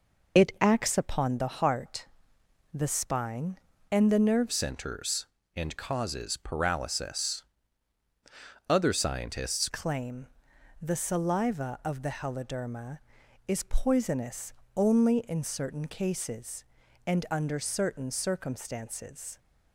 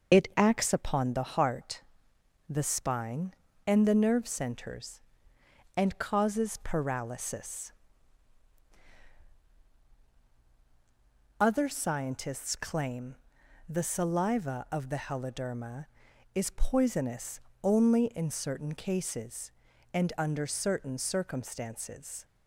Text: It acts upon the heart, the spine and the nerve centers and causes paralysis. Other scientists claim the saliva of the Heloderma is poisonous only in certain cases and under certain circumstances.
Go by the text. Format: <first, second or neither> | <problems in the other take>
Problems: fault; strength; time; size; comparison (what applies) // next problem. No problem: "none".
second | changes voice from "centers" to "scientists"; from 4.5 to 9.6 s; 5.1 s long // pauses between "claim" and "the"; noticeable; at 10.2 s; 0.56 s long; noticeable in the second // pauses between "poisonous" and "only"; slight; at 14.5 s; 0.24 s long; slight in the second